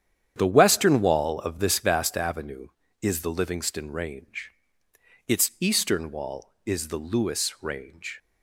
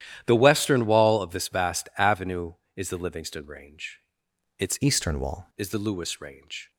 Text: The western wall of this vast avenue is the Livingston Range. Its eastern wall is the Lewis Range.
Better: first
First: starts louder than the rest; strong; until 1.3 s; 9 dB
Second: starts louder than the rest; strong; until 1.2 s; 11.5 dB // changes voice from "eastern" to "wall"; from 4.8 to 5.4 s; 0.6 s long

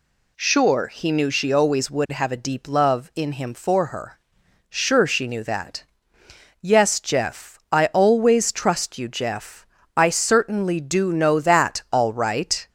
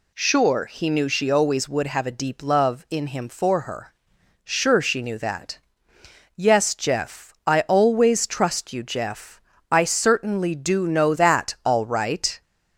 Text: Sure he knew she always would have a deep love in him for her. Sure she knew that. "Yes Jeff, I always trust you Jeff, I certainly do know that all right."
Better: neither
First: none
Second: none

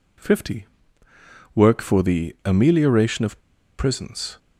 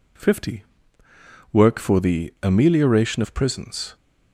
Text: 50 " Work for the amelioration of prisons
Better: second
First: pauses between "of" and "prisons"; at 3.3 s; 0.39 s long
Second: none

